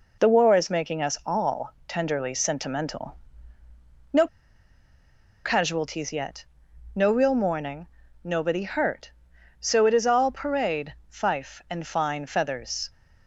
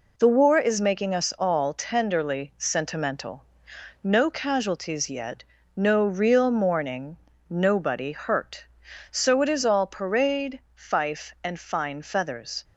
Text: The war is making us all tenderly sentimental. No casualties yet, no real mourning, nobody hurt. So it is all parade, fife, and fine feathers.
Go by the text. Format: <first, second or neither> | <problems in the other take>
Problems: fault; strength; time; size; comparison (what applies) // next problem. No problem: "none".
second | pauses between "No" and "casualties"; at 4.2 s; 1.1 s long